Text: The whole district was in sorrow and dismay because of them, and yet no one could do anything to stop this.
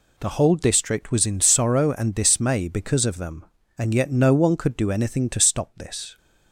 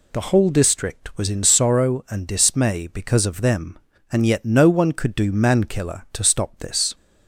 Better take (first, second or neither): first